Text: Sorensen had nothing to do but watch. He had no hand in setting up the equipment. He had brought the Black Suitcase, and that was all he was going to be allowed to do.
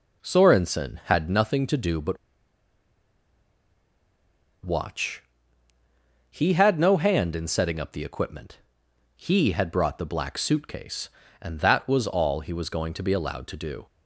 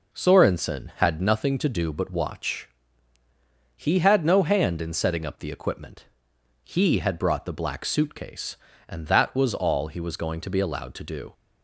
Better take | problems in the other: second | pauses between "but" and "watch"; strong; at 2.1 s; 2.4 s long

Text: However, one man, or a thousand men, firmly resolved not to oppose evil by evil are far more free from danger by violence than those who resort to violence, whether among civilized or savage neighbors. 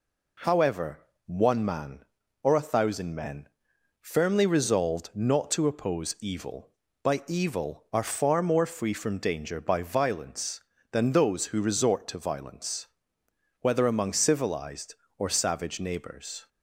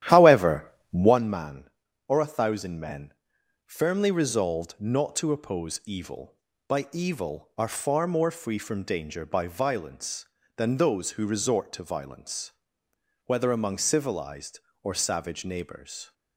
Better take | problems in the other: first | starts louder than the rest; strong; until 1.2 s; 12 dB

